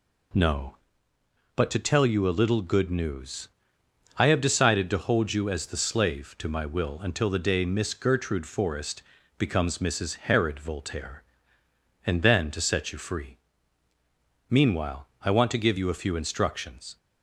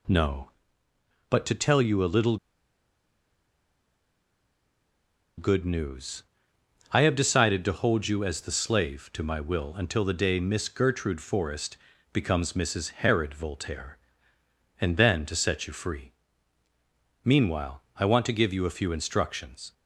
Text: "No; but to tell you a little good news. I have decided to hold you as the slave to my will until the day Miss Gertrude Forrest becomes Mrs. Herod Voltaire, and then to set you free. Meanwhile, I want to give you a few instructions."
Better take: first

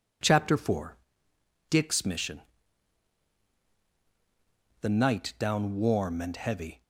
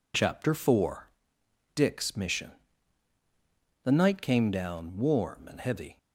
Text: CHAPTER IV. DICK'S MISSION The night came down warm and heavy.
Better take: second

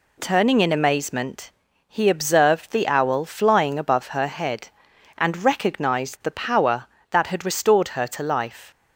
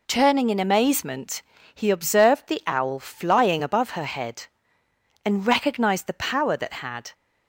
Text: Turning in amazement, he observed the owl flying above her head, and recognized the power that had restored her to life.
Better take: first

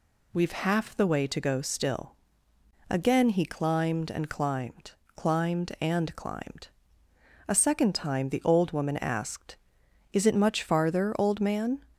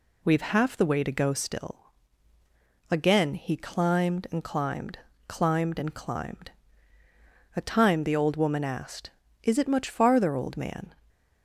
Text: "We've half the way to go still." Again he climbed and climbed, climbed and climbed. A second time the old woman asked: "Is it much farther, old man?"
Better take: first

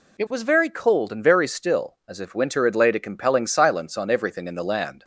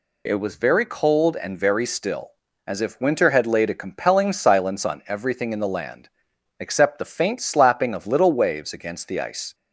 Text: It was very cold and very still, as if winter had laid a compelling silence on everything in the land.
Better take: first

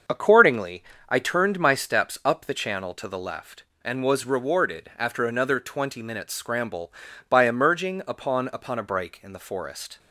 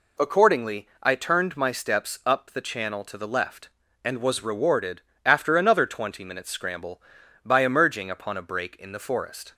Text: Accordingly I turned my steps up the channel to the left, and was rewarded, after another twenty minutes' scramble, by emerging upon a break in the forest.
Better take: second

